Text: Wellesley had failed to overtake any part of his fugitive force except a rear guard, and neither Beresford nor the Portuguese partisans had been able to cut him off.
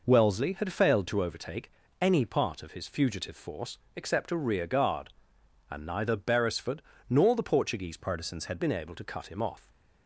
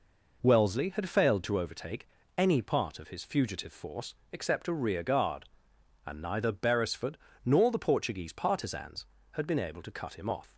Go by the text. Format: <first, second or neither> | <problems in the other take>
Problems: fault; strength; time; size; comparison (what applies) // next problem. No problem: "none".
second | pauses between "overtake" and "any"; slight; at 1.7 s; 0.28 s long; slight in the second // pauses between "force" and "except"; slight; at 3.7 s; 0.18 s long; slight in the second // pauses between "Beresford" and "nor"; slight; at 6.8 s; 0.26 s long; slight in the second // changes voice from "partisans" to "had"; from 7.9 to 8.5 s; 0.6 s long